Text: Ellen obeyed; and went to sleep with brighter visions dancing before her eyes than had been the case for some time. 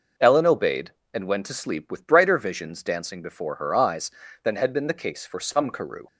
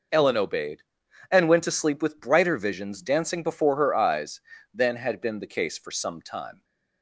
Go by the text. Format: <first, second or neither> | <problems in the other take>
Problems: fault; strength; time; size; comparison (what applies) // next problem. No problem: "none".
second | says "karoo" for "time"; at 5.6 s